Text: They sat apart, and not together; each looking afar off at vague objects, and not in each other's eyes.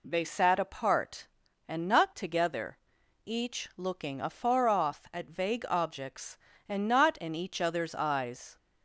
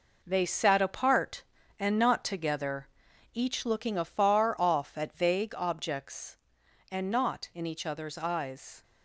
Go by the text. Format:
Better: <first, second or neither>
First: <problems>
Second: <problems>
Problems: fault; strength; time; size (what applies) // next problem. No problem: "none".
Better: first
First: none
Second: gets quieter; strong; throughout; 7.5 dB